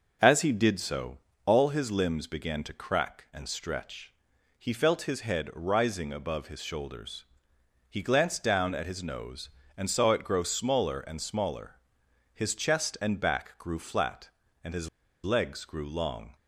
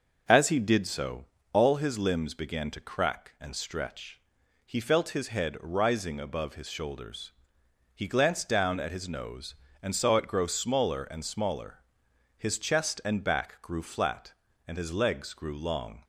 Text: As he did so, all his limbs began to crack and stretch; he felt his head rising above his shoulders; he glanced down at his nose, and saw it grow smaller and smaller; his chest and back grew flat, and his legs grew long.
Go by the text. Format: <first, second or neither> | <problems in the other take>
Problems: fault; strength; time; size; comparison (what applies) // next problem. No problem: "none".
second | starts louder than the rest; noticeable; until 1.4 s; 6 dB // pauses between "his" and "legs"; slight; at 14.8 s; 0.36 s long